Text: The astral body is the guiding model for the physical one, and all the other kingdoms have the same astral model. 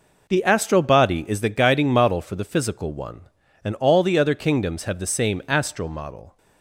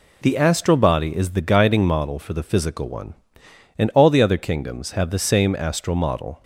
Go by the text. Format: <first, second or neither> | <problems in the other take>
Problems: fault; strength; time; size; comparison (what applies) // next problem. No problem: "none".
neither | none